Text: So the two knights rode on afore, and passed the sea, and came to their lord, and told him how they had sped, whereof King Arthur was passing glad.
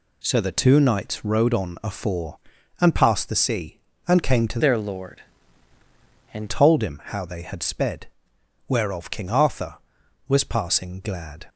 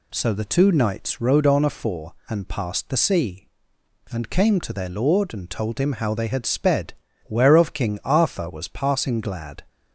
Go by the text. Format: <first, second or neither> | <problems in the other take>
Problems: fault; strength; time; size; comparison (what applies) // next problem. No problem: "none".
second | changes voice from "their" to "and"; from 4.5 to 6.4 s; 1.9 s long